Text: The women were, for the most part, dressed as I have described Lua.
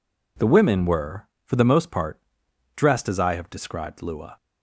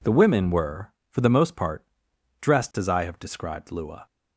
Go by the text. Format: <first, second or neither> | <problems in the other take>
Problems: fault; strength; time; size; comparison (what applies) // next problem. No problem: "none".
neither | none